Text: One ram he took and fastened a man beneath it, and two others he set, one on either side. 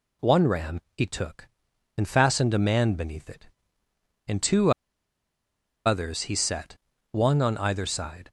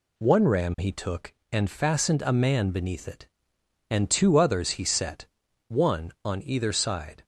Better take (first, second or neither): second